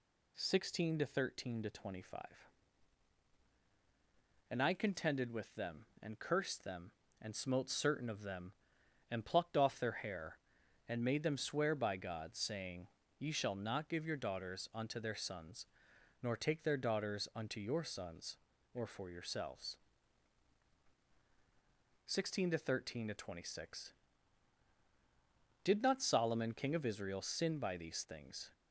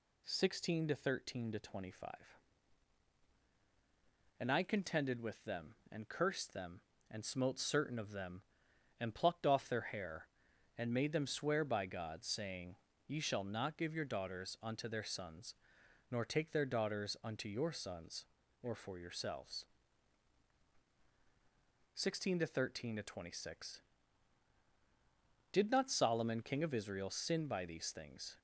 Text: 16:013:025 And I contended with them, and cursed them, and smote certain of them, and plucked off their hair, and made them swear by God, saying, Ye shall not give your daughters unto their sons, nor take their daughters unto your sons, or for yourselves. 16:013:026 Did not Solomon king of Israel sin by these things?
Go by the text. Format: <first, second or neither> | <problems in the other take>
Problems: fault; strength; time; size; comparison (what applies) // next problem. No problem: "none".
neither | none